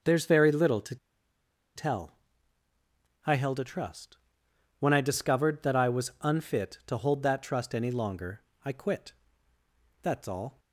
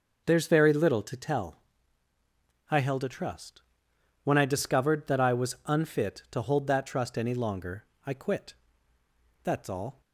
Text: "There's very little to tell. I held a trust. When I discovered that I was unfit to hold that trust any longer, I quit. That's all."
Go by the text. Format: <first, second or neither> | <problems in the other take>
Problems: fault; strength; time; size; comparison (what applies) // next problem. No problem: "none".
second | pauses between "to" and "tell"; noticeable; at 0.9 s; 0.79 s long